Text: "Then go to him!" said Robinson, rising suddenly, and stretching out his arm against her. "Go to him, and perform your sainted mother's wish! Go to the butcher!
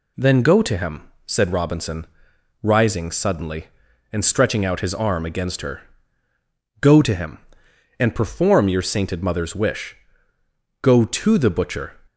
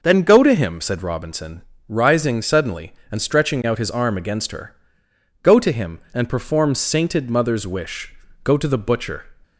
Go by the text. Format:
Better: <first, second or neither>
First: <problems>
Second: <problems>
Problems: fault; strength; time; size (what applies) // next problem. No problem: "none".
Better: first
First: none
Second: skips "your"; at 6.7 s